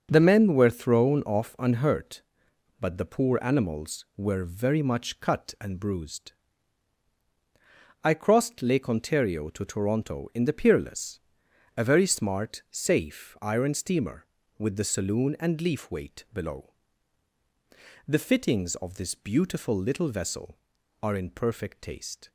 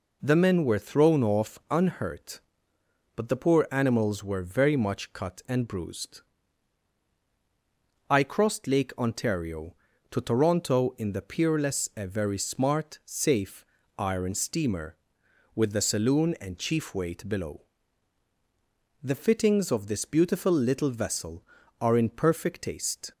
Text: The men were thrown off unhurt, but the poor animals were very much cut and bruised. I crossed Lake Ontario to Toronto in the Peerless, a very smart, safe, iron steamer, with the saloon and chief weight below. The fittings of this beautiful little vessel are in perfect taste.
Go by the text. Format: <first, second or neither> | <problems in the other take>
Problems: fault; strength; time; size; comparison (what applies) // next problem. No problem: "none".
second | starts louder than the rest; until 1.1 s; 6.5 dB // says "leaf" for "chief"; at 15.6 s